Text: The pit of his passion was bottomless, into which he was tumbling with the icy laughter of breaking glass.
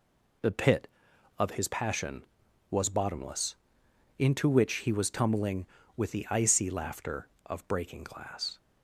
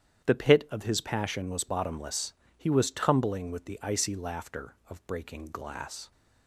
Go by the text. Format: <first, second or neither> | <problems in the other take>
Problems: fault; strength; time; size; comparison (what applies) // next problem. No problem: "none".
first | starts louder than the rest; strong; until 1.3 s; 9.5 dB // skips "into which"; at 2.4 s